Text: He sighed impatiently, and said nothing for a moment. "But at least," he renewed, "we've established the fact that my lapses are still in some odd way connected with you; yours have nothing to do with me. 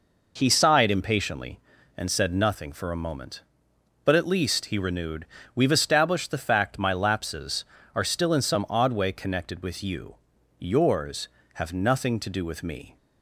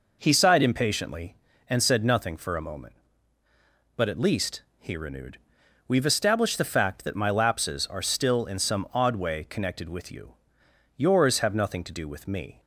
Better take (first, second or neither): second